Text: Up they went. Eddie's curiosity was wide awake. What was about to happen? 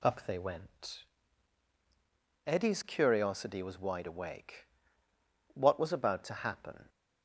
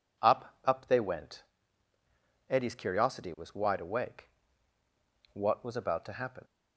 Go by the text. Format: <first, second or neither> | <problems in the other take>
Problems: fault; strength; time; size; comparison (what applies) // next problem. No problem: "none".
first | says "Up" twice; at 0.6 s